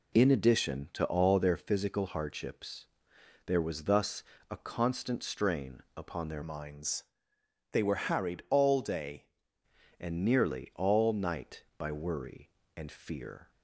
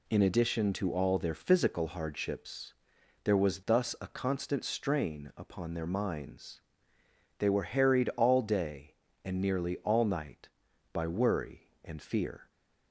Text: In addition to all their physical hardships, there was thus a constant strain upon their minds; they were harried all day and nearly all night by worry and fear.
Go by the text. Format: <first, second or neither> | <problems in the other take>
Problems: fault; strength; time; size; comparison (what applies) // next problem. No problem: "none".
second | pauses between "thus" and "a"; slight; at 4.2 s; 0.26 s long // changes voice from "minds" to "day"; from 6.4 to 9.2 s; 2.8 s long